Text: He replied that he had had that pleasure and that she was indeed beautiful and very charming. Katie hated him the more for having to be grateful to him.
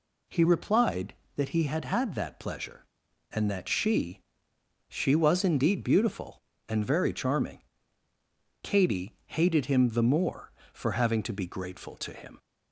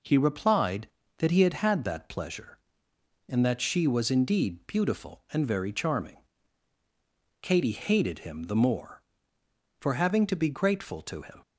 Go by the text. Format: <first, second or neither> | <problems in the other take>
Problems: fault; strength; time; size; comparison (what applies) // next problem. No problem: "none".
second | says "she" twice; at 4.8 s